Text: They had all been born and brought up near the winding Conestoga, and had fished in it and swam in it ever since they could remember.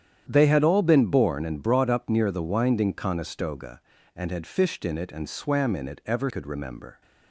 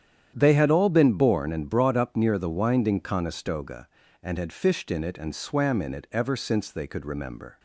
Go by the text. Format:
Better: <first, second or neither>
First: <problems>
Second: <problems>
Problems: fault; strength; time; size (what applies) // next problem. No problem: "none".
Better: second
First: starts louder than the rest; strong; until 1.3 s; 9.5 dB // skips "since they"; at 6.2 s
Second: starts louder than the rest; strong; until 1.3 s; 9.5 dB